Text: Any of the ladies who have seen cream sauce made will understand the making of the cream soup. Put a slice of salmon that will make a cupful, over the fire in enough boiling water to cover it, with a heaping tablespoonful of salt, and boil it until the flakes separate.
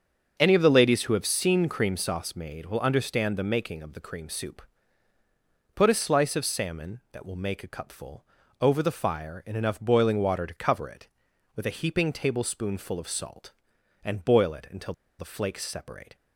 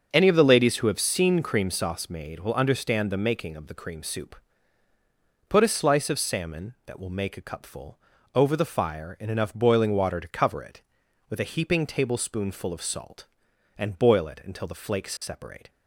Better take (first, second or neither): second